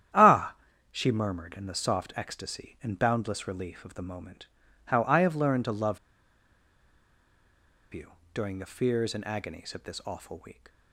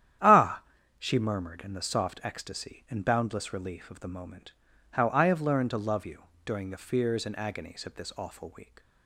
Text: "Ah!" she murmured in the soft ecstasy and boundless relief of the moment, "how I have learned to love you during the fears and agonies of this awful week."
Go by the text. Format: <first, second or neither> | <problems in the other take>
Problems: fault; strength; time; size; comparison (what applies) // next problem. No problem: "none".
second | starts louder than the rest; strong; until 1.5 s; 10.5 dB; strong in the second // pauses between "love" and "you"; strong; at 5.9 s; 1.9 s long // pauses between "you" and "during"; slight; at 8.1 s; 0.20 s long; slight in the second